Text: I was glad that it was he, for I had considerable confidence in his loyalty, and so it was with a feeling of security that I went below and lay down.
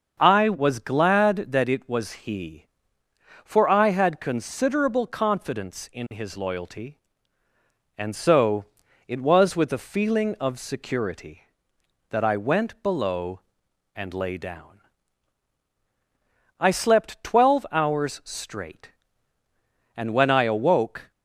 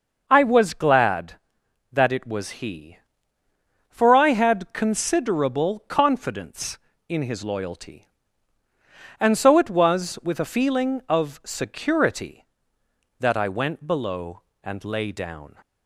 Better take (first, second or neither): second